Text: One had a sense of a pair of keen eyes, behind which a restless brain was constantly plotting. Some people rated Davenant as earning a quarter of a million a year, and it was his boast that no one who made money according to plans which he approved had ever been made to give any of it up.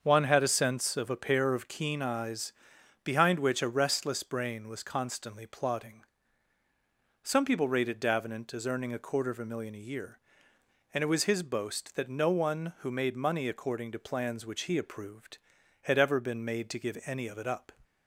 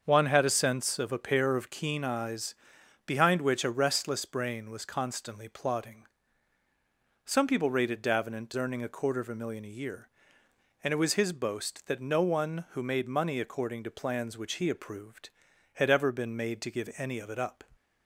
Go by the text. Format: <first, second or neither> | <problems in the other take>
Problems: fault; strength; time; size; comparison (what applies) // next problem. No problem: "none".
first | starts louder than the rest; until 1.0 s; 7 dB; also in the first // skips "as"; at 8.5 s